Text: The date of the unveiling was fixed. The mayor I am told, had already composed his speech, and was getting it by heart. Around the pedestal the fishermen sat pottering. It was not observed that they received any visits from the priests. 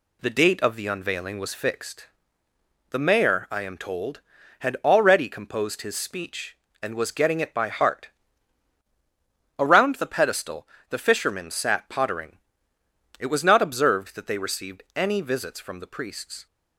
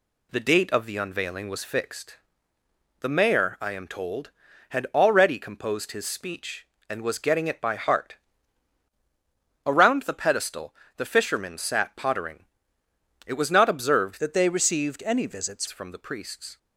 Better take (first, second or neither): first